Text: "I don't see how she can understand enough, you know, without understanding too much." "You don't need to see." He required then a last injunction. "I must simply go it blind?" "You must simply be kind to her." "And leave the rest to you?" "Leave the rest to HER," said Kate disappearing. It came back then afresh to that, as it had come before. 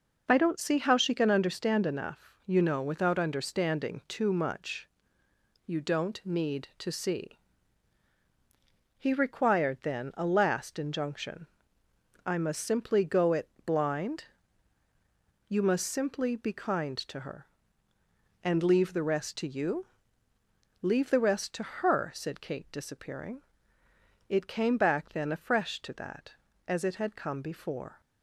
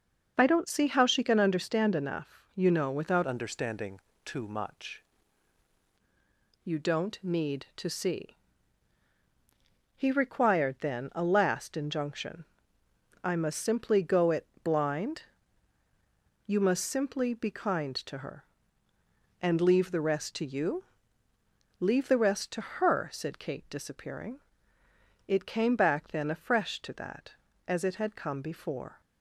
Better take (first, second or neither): first